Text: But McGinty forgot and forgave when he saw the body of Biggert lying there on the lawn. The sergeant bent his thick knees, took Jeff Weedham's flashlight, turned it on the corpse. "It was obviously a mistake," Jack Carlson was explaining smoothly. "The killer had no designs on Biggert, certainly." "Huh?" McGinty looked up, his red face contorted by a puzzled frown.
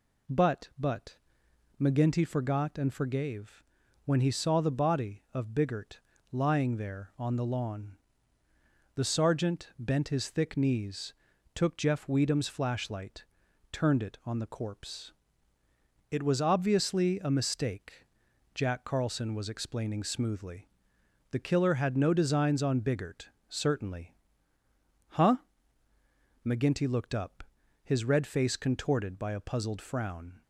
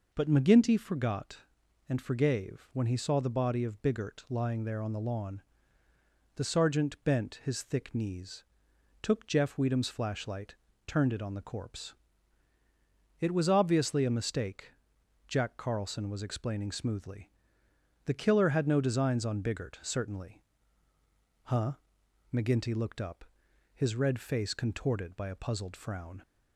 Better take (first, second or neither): second